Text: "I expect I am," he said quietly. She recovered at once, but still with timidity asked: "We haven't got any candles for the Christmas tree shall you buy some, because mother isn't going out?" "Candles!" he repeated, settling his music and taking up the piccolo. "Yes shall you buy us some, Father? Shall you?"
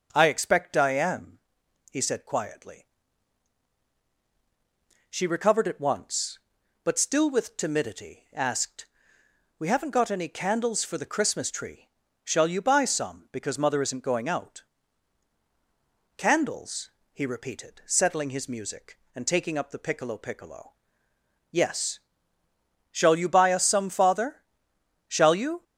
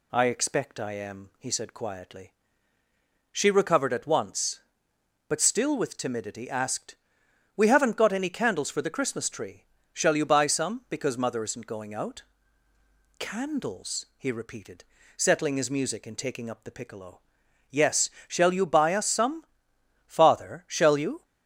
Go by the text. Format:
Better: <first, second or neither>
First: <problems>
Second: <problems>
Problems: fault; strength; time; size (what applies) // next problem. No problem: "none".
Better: second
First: pauses between "tree" and "shall"; at 11.8 s; 0.38 s long // says "piccolo" twice; at 20.1 s // pauses between "Yes" and "shall"; noticeable; at 21.9 s; 0.94 s long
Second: pauses between "tree" and "shall"; slight; at 9.6 s; 0.28 s long // pauses between "Yes" and "shall"; slight; at 18.0 s; 0.20 s long